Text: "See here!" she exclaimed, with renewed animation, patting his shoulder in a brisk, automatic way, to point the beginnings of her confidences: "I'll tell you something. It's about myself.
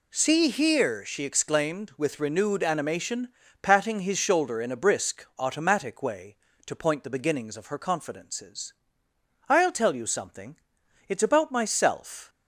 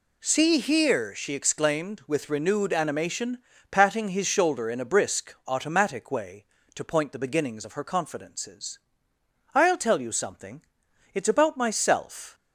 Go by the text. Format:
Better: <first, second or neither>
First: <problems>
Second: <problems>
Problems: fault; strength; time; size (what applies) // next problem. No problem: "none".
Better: neither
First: none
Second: none